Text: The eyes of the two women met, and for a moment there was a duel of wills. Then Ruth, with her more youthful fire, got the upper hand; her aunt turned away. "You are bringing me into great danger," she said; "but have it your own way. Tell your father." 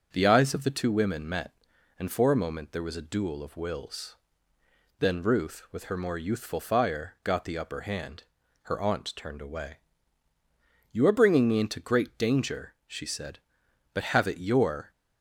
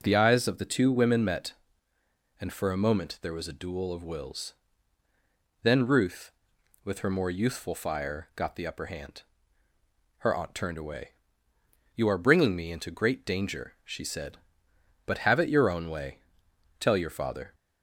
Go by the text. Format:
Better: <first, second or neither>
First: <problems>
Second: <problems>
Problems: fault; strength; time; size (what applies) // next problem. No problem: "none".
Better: second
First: starts louder than the rest; until 1.1 s; 6.5 dB // stops before "own way Tell your father"; at 14.9 s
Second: none